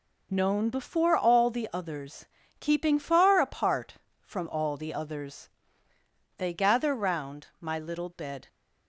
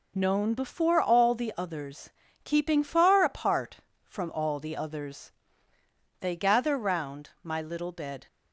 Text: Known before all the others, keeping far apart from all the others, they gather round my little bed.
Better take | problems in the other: neither | none

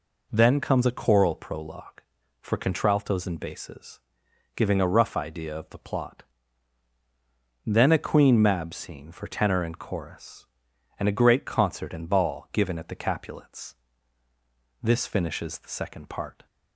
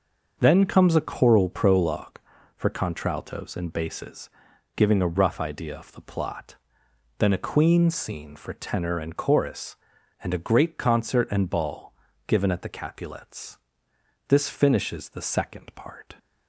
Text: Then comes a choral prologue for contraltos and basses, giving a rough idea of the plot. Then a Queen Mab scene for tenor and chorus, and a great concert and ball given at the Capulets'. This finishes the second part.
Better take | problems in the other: first | starts louder than the rest; until 1.4 s; 6 dB // skips "Mab"; at 7.8 s // pauses between "ball" and "given"; slight; at 11.9 s; 0.34 s long

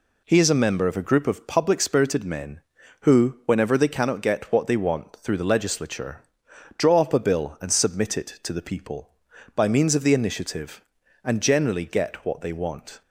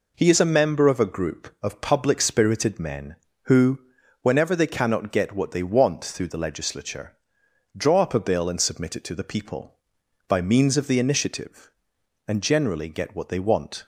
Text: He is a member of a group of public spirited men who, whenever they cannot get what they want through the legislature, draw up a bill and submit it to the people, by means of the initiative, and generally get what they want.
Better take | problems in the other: neither | none

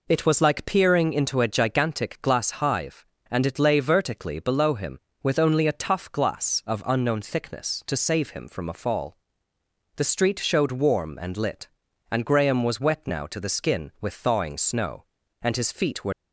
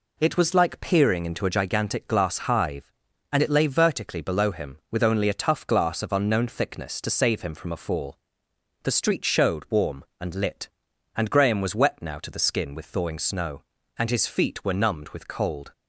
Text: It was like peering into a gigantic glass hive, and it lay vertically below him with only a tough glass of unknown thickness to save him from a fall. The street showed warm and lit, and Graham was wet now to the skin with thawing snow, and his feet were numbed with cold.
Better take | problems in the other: second | stops before "numbed with cold"; at 16.1 s

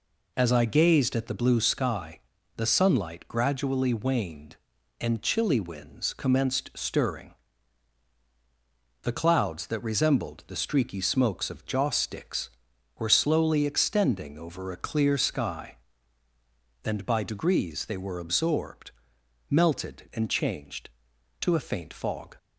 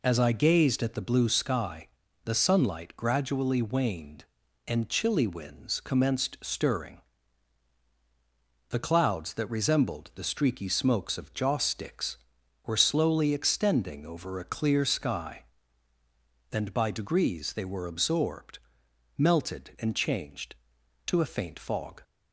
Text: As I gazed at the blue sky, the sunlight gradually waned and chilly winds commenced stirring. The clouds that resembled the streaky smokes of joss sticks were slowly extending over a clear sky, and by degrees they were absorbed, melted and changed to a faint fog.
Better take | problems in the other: neither | none

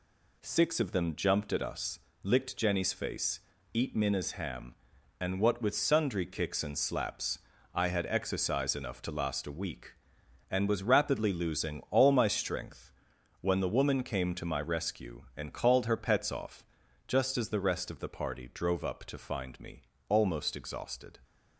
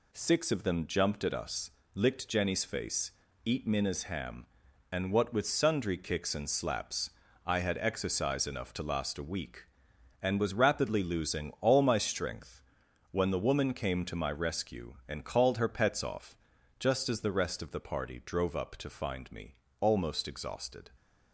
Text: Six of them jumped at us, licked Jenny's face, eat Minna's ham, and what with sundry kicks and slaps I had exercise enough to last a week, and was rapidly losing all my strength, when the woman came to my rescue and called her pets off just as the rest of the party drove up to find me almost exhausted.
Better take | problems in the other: neither | pauses between "slaps" and "I"; slight; the same in both // pauses between "off" and "just"; the same in both // pauses between "me" and "almost"; slight; the same in both

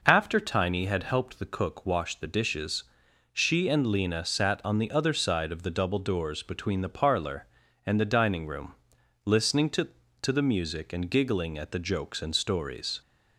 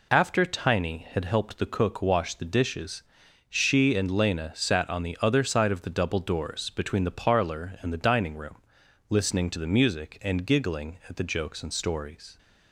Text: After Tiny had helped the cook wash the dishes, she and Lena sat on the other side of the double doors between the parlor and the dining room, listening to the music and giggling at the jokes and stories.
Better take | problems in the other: second | says "to" twice; at 10.2 s

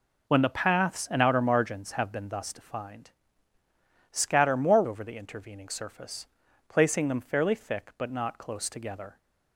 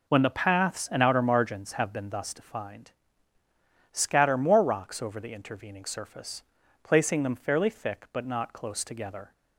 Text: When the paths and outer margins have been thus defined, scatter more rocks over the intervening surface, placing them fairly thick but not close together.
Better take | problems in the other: second | skips "rocks"; at 4.8 s

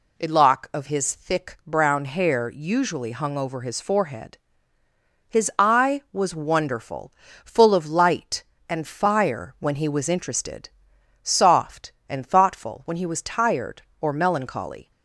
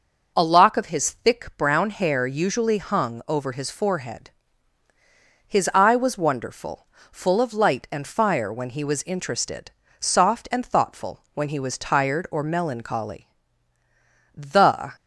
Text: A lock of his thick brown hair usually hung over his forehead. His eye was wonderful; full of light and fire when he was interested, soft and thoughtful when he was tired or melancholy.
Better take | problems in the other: first | goes on to say "The"; from 14.3 s on; 0.56 s long

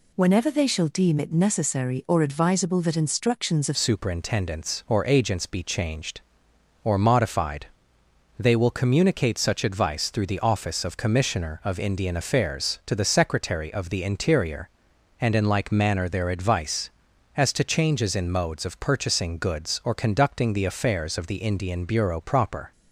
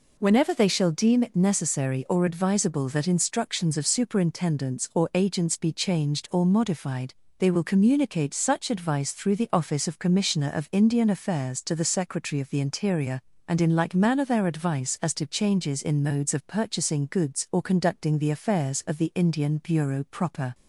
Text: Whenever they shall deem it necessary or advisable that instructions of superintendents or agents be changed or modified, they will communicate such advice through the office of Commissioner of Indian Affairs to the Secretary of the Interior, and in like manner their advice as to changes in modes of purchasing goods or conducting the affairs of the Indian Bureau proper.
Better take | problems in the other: second | changes voice at "superintendents"; from 3.7 s on; 19.0 s long

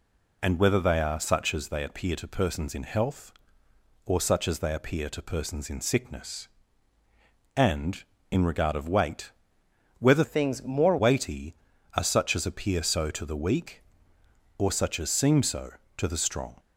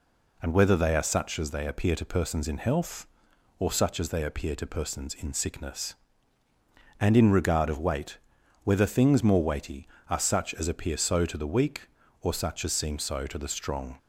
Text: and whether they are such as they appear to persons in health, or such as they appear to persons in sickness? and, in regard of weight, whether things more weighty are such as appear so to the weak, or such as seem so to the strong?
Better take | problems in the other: second | changes voice from "things" to "more"; from 10.2 to 10.9 s; 0.7 s long

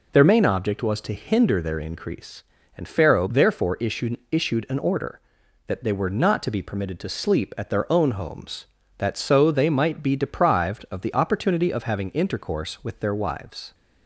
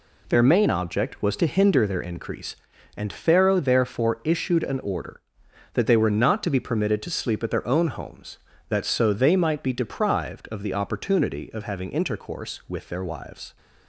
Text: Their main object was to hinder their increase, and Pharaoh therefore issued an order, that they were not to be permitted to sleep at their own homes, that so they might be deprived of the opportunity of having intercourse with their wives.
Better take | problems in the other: second | says "issued" twice; at 4.3 s

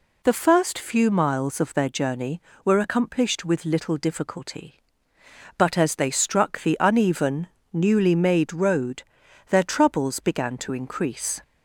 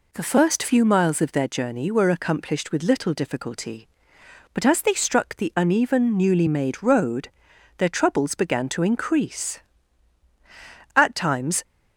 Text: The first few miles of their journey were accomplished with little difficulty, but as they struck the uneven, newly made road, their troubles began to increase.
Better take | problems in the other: first | goes on to say "At times"; noticeable; from 10.9 s on; 0.66 s long

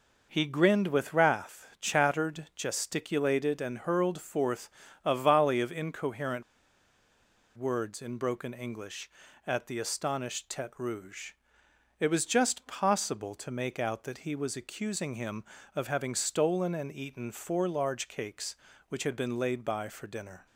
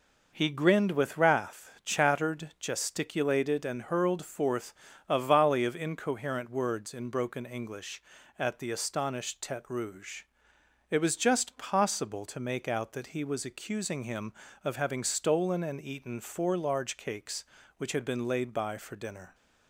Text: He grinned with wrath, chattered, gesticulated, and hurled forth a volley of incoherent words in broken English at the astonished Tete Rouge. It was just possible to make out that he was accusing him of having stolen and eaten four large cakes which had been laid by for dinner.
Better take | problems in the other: second | pauses between "forth" and "a"; slight; at 4.6 s; 0.34 s long; slight in the second // pauses between "incoherent" and "words"; at 6.4 s; 1.1 s long

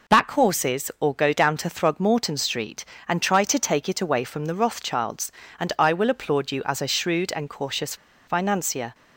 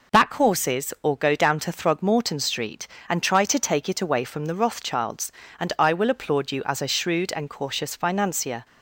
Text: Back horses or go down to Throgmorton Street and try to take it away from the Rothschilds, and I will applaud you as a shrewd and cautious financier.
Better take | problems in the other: second | pauses between "cautious" and "financier"; slight; at 7.9 s; 0.32 s long

